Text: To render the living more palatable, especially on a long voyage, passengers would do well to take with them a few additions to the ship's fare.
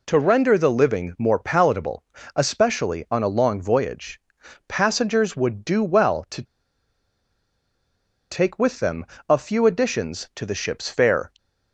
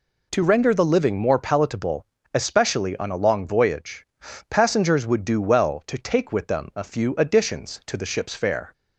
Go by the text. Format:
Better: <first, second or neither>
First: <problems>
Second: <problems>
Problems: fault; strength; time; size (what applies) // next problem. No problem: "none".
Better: second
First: pauses between "to" and "take"; strong; at 6.4 s; 1.8 s long // pauses between "them" and "a"; slight; at 9.0 s; 0.24 s long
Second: none